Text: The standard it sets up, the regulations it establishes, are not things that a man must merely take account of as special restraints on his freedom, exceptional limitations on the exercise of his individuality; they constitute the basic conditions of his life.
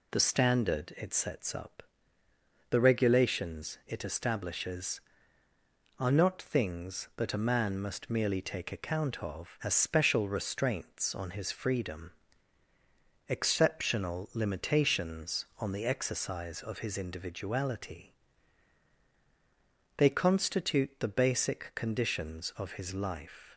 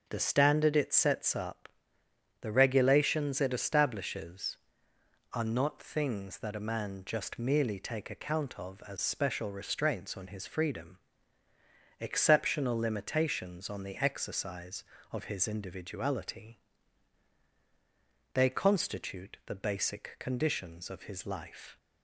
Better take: first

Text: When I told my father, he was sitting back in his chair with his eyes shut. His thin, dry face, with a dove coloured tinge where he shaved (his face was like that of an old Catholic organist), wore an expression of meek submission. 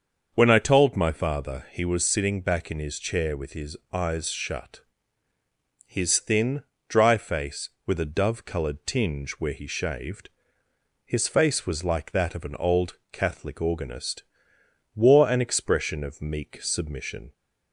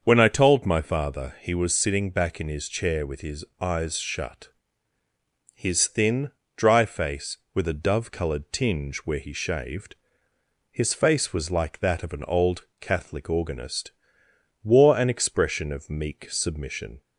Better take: neither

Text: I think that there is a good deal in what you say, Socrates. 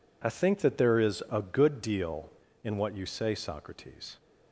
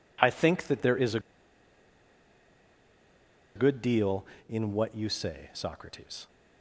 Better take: first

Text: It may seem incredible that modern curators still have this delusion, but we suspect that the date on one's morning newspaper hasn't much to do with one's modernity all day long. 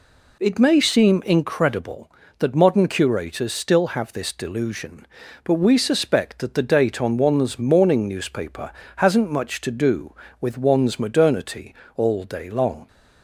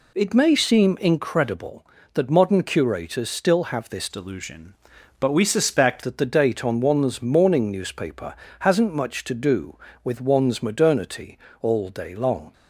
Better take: first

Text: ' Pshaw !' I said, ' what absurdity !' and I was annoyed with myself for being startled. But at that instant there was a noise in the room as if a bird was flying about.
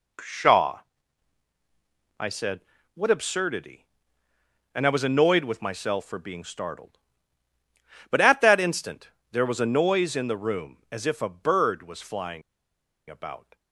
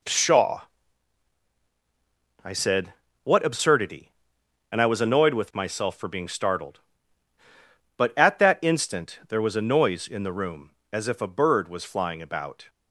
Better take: second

